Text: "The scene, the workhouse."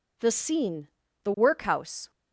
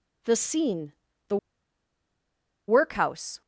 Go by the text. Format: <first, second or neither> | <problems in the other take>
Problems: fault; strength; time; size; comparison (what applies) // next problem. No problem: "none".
first | pauses between "the" and "workhouse"; strong; at 1.3 s; 1.3 s long